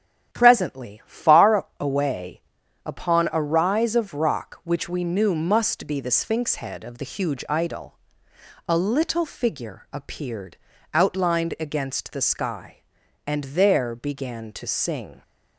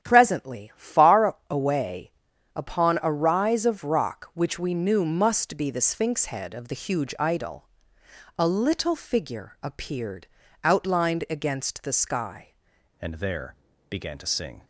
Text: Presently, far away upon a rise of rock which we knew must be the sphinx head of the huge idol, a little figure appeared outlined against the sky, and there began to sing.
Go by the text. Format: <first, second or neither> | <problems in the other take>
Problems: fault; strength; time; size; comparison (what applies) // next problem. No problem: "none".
first | starts louder than the rest; strong; until 1.0 s; 9.5 dB; strong in the first // pauses between "away" and "upon"; at 2.1 s; 0.44 s long; also in the first // pauses between "appeared" and "outlined"; slight; at 10.2 s; 0.36 s long; slight in the first // changes voice at "and"; from 13.0 s on; 1.6 s long // pauses between "there" and "began"; slight; at 13.5 s; 0.34 s long